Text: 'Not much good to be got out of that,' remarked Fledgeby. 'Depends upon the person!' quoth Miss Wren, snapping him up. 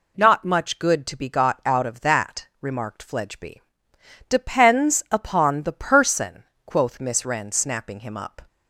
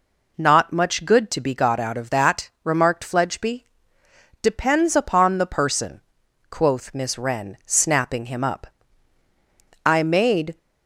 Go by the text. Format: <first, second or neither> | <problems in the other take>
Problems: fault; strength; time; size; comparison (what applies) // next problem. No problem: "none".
first | goes on to say "I made"; noticeable; from 9.8 s on; 0.72 s long